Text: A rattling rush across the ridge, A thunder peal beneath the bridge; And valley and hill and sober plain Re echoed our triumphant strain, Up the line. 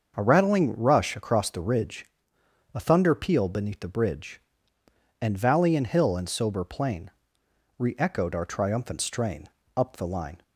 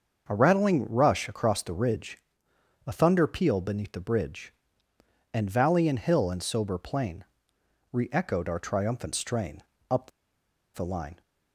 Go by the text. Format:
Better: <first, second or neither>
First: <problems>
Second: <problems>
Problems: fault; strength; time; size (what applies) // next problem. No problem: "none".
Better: first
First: starts louder than the rest; until 1.1 s; 6.5 dB // pauses between "plain" and "Re"; noticeable; at 7.0 s; 0.70 s long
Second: starts louder than the rest; until 1.2 s; 6.5 dB // pauses between "plain" and "Re"; noticeable; at 7.2 s; 0.70 s long // pauses between "Up" and "the"; noticeable; at 10.1 s; 0.64 s long